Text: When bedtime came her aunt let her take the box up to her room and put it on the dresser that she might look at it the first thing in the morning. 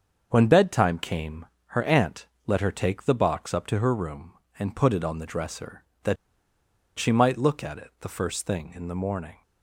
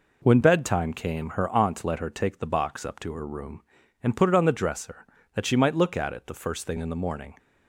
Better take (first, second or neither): second